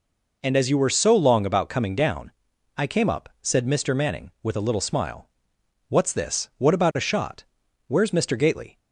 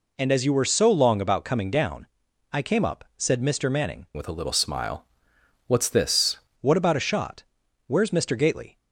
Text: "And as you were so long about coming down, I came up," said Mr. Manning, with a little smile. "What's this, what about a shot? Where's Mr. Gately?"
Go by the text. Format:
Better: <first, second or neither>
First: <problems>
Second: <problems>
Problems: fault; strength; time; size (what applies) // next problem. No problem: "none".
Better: first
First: none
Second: changes voice from "with" to "this"; from 4.1 to 6.3 s; 2.2 s long